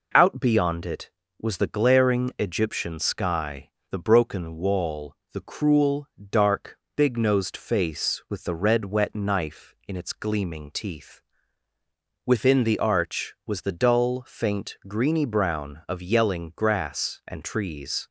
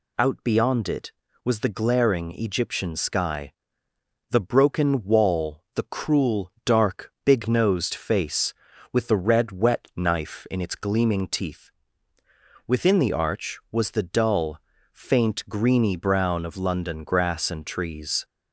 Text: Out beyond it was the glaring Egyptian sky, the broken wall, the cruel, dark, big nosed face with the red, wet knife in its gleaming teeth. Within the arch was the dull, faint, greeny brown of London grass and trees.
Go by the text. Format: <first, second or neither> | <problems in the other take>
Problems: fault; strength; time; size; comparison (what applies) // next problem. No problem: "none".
second | says "Yelling" for "London"; at 16.0 s